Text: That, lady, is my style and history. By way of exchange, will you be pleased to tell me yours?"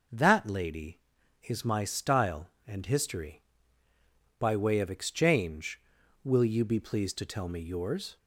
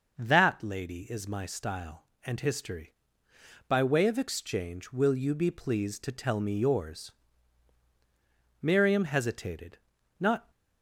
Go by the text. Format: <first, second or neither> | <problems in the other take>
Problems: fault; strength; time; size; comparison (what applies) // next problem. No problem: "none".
first | goes on to say "Miriam hesitated not"; strong; from 8.5 s on; 1.9 s long